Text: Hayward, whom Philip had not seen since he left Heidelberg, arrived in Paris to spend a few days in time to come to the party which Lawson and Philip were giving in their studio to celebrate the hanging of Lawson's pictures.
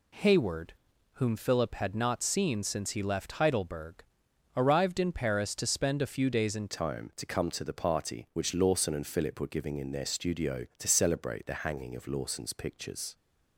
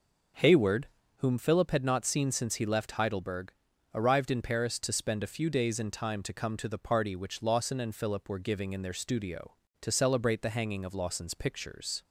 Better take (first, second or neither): second